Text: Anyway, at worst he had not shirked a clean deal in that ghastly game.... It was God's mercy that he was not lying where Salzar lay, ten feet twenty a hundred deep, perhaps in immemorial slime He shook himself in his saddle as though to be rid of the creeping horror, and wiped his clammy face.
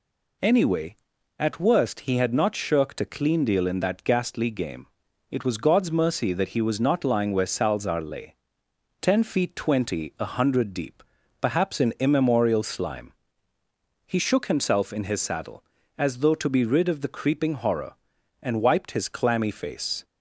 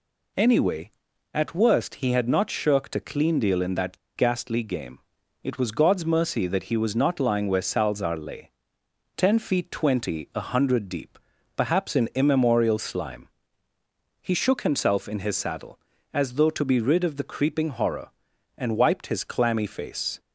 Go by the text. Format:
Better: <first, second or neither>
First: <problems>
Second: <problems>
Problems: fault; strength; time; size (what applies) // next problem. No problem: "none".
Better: first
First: pauses between "slime" and "He"; noticeable; at 13.1 s; 0.92 s long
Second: pauses between "that" and "ghastly"; slight; at 3.9 s; 0.18 s long // pauses between "slime" and "He"; noticeable; at 13.2 s; 0.92 s long